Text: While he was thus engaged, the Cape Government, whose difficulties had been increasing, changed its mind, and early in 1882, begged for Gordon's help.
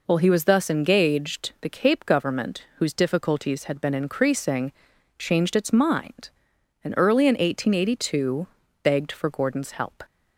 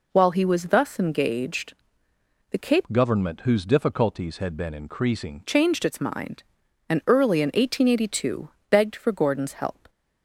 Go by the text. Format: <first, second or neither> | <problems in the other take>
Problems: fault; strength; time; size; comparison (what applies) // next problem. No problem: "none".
first | changes voice from "Government" to "increasing"; from 2.9 to 5.4 s; 2.5 s long